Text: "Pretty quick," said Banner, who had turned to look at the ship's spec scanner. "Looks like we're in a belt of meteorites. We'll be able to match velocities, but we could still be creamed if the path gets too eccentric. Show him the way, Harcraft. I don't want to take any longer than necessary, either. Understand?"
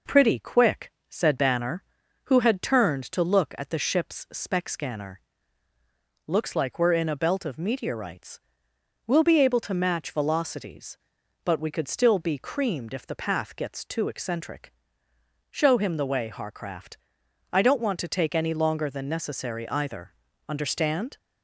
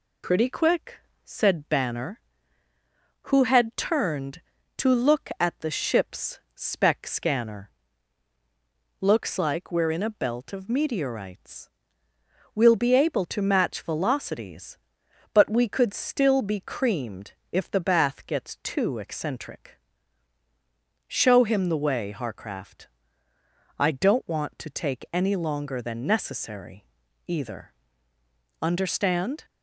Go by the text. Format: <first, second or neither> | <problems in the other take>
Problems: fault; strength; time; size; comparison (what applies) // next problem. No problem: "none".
first | pauses between "ship's" and "spec"; slight; at 6.3 s; 0.16 s long // pauses between "creamed" and "if"; slight; at 17.3 s; 0.18 s long // says "bath" for "path"; at 17.8 s